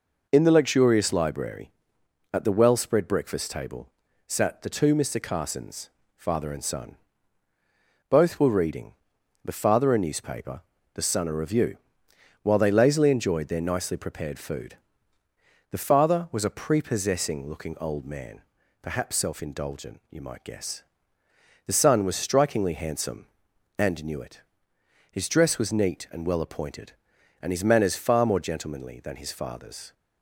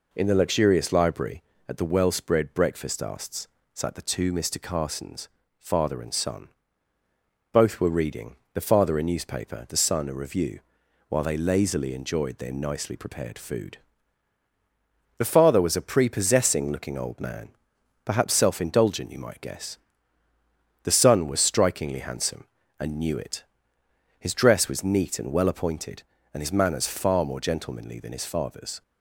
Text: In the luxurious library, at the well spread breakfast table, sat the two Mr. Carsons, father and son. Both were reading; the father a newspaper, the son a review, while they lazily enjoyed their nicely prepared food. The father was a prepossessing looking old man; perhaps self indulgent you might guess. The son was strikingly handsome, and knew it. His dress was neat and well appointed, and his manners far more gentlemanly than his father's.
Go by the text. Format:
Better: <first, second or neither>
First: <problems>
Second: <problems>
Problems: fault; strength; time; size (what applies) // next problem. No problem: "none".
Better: first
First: none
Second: says "asts" for "table"; at 3.0 s